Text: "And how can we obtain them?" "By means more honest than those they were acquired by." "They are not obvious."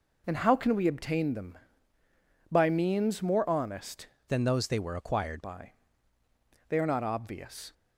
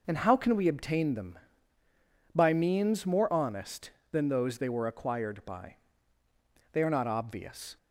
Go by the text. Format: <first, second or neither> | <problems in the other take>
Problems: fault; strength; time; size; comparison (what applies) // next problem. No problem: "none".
second | changes voice from "than" to "acquired"; from 4.2 to 5.4 s; 1.2 s long